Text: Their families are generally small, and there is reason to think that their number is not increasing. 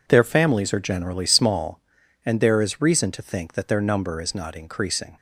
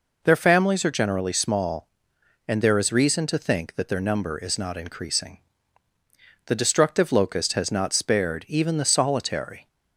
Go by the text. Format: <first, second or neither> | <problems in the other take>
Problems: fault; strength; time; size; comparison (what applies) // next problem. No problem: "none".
first | goes on to say "The destructive locust has not spared even the solitary"; strong; from 6.4 s on; 3.2 s long